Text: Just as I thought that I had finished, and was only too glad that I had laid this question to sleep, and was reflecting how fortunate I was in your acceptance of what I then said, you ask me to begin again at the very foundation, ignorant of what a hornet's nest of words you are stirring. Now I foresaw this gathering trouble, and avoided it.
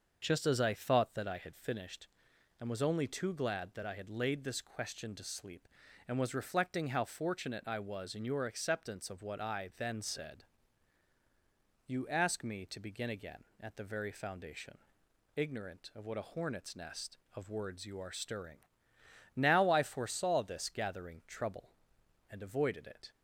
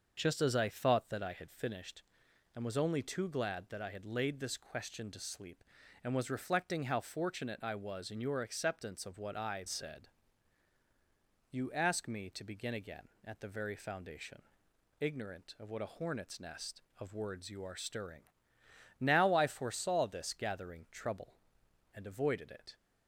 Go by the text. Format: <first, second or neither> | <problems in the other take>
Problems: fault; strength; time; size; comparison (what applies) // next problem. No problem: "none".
first | starts louder than the rest; until 1.1 s; 6.5 dB; also in the first // skips "then"; at 9.6 s